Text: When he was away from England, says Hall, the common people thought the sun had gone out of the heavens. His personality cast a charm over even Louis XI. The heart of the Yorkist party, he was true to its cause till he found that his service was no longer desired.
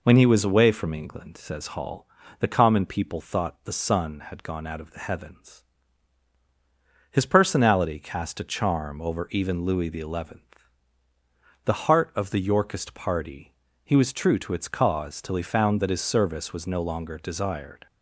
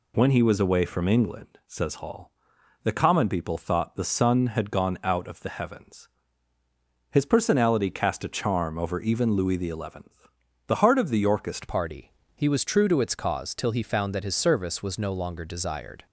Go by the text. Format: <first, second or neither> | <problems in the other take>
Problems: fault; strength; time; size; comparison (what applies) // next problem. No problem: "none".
first | changes voice at "party"; from 11.6 s on; 4.4 s long